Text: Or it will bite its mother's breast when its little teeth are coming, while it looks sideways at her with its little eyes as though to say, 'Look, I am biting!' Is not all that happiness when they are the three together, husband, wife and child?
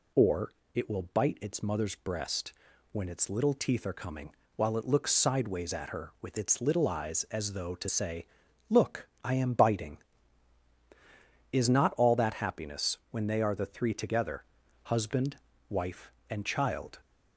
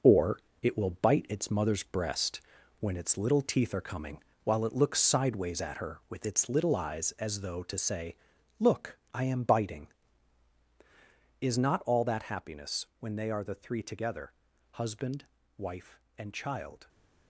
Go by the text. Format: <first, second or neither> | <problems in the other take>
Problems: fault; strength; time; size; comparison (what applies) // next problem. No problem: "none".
first | gets quieter; strong; throughout; 7.5 dB // pauses between "Or" and "it"; slight; at 0.3 s; 0.24 s long; slight in the first // pauses between "breast" and "when"; at 2.4 s; 0.38 s long; also in the first